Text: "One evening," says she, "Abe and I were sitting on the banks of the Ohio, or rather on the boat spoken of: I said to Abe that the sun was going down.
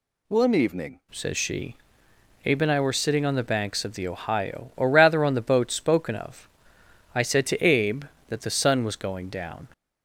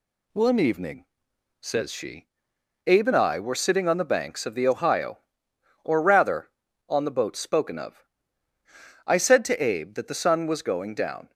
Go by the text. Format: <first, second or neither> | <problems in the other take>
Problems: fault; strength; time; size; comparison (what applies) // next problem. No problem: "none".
second | changes voice at "says"; from 1.0 s on; 8.6 s long